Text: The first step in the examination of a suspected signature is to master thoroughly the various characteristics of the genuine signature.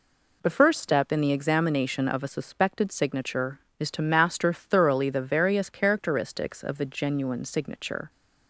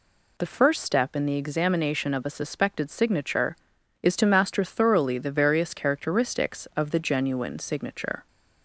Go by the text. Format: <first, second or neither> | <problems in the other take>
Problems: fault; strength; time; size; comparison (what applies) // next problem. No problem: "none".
neither | none